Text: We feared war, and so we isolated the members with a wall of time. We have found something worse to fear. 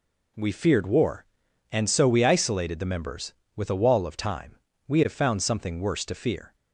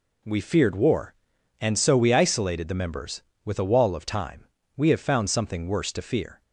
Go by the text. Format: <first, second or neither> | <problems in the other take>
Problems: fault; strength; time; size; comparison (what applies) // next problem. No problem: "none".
neither | none